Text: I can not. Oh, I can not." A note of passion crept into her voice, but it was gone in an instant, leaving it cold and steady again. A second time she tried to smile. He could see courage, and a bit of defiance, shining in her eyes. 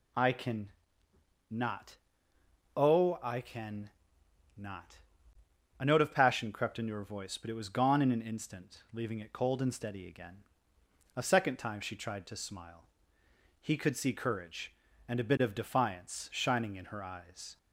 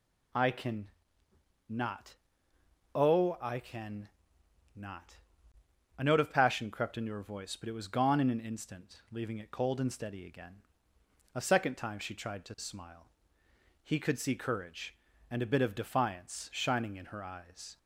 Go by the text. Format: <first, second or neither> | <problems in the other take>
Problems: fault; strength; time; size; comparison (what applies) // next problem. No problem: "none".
neither | pauses between "can" and "not"; noticeable; the same in both // pauses between "can" and "not"; noticeable; the same in both